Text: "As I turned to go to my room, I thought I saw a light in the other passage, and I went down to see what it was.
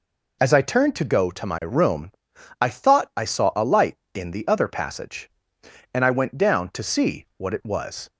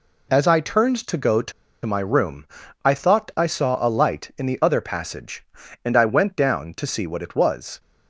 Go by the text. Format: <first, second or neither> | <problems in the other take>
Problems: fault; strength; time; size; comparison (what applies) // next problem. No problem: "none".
first | pauses between "to" and "my"; slight; at 1.5 s; 0.33 s long